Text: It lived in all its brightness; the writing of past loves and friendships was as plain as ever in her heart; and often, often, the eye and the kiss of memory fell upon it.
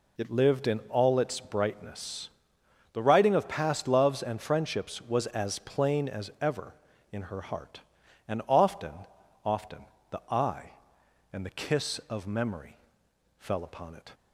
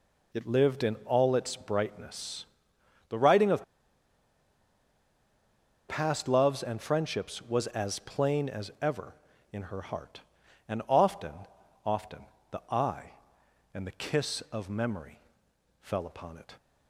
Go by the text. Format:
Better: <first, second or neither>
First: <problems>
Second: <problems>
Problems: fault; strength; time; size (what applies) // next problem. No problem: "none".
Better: first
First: pauses between "memory" and "fell"; noticeable; at 12.7 s; 0.62 s long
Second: pauses between "of" and "past"; strong; at 3.6 s; 2.2 s long // pauses between "memory" and "fell"; noticeable; at 15.2 s; 0.62 s long